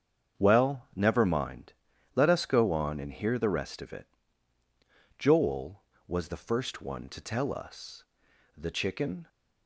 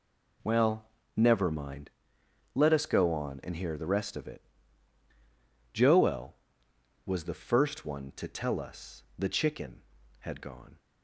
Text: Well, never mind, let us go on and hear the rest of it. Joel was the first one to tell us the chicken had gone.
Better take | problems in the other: second | starts louder than the rest; strong; until 1.4 s; 7.5 dB // pauses between "us" and "the"; noticeable; at 8.0 s; 0.52 s long // stops before "had gone"; at 9.2 s

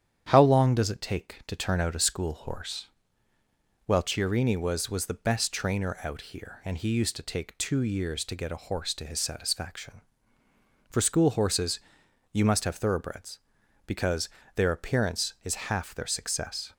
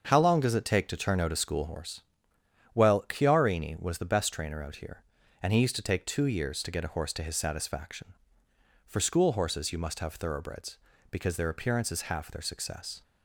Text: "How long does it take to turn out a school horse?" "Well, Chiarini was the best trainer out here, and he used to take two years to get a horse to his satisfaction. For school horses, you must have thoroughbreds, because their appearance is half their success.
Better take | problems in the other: second | starts louder than the rest; strong; until 1.2 s; 9 dB; also in the second // says "was" twice; at 4.8 s // pauses between "because" and "their"; slight; at 14.2 s; 0.28 s long

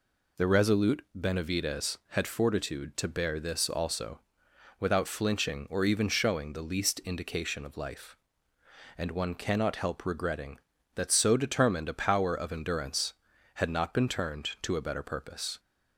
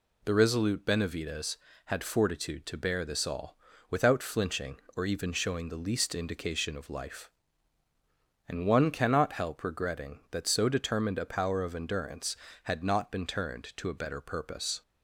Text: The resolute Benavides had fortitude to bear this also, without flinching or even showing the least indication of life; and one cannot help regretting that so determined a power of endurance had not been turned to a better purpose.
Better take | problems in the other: first | says "all" for "also"; at 3.2 s

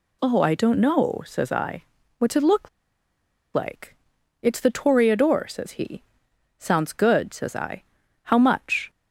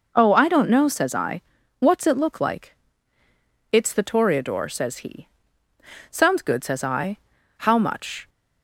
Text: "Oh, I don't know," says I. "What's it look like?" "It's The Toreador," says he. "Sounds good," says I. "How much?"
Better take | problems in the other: second | pauses between "look" and "like"; noticeable; at 2.6 s; 0.85 s long

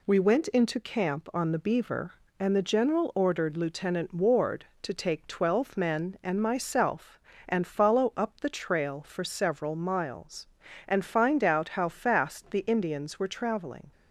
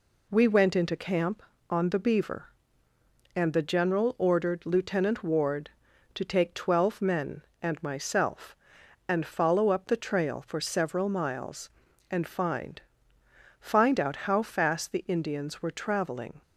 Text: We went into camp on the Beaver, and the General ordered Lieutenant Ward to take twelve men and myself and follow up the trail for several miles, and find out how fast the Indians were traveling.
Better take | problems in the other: first | says "find" twice; at 13.6 s

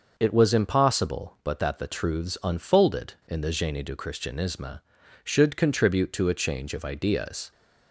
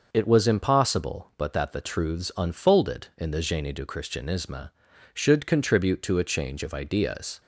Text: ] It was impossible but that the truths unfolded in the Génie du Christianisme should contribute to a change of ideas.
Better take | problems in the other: neither | none

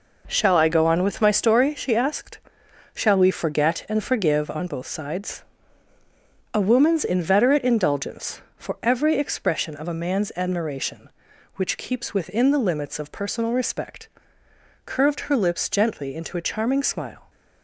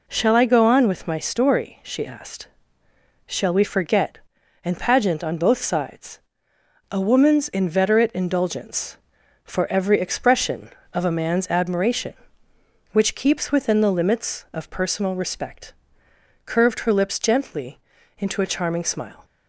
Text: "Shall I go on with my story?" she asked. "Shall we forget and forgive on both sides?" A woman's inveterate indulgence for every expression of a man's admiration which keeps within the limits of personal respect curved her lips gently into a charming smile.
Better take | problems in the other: first | says "pageant" for "forgive"; at 4.7 s // pauses between "respect" and "curved"; noticeable; at 15.7 s; 0.72 s long; noticeable in the first // pauses between "gently" and "into"; at 17.8 s; 0.38 s long

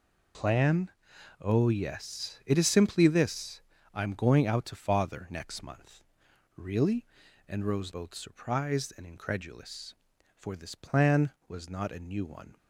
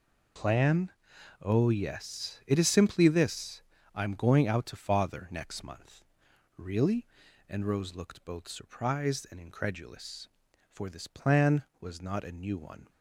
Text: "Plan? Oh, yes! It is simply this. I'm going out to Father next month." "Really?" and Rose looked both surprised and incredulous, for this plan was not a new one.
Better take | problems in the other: second | skips "looked"; at 7.9 s

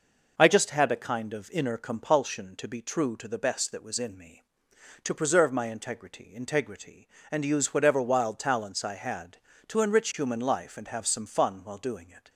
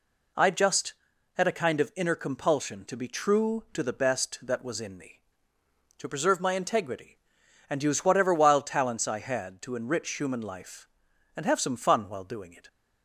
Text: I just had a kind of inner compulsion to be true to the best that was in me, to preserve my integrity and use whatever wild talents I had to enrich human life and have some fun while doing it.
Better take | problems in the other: second | says "integrity" twice; at 6.3 s

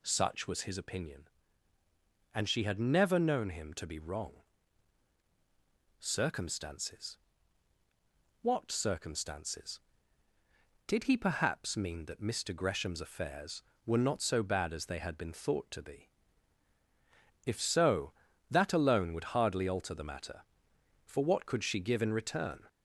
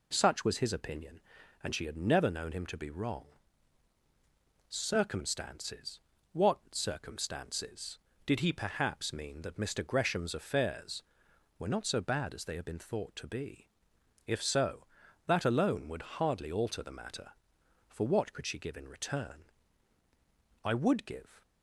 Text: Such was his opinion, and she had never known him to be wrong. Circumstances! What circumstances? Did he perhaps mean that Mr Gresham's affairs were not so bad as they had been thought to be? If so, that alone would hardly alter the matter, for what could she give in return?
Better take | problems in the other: first | goes on to say "I would give"; noticeable; from 20.6 s on; 0.80 s long

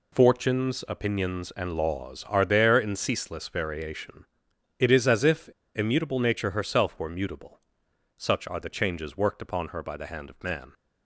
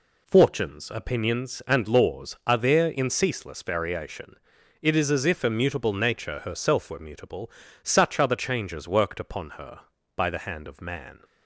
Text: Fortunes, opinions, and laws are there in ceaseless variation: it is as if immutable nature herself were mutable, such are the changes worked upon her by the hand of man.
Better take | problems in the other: second | pauses between "if" and "immutable"; slight; at 5.4 s; 0.27 s long

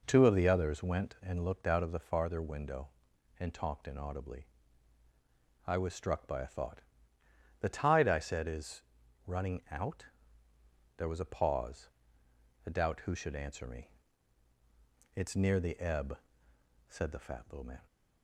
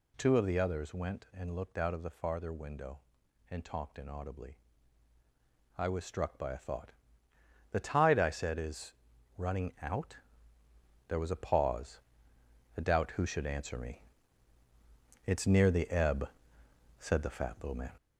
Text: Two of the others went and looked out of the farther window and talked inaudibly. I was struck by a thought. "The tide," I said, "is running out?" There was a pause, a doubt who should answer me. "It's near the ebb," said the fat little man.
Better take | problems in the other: first | gets louder; noticeable; throughout; 6 dB // pauses between "is" and "running"; at 8.9 s; 0.44 s long; also in the first

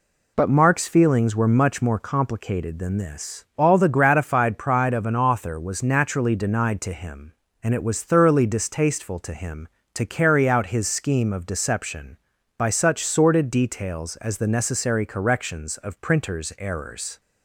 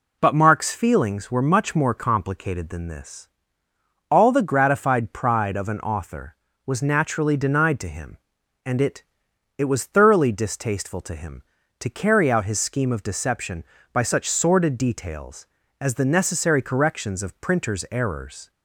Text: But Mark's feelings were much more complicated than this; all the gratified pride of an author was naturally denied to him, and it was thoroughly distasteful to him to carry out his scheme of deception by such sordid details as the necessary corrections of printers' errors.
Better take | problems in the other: first | says "it" twice; at 9.5 s

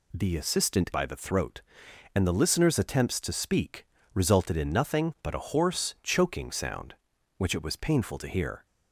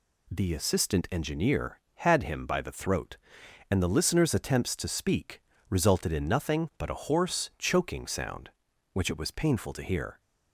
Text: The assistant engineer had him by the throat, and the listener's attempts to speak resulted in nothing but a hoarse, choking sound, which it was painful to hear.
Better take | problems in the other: second | skips "engineer had him"; at 0.9 s // pauses between "speak" and "resulted"; slight; at 3.8 s; 0.30 s long; slight in the second

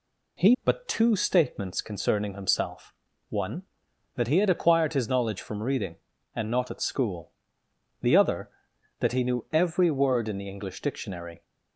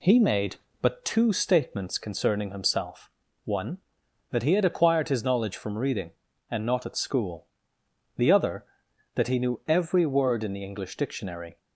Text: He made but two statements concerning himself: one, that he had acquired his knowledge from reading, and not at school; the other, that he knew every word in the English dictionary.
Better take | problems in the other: second | skips "made"; at 0.5 s

